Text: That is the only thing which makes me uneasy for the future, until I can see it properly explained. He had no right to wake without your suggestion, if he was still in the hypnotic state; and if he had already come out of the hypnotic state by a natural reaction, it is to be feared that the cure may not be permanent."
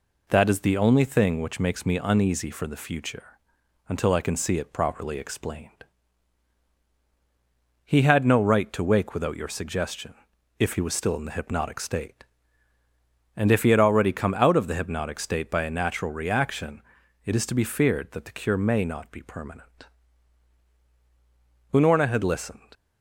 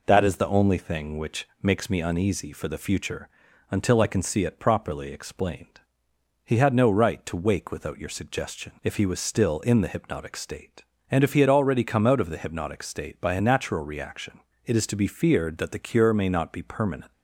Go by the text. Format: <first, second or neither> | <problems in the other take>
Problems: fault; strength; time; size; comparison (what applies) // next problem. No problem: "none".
second | goes on to say "Unorna had listened"; noticeable; from 21.7 s on; 0.96 s long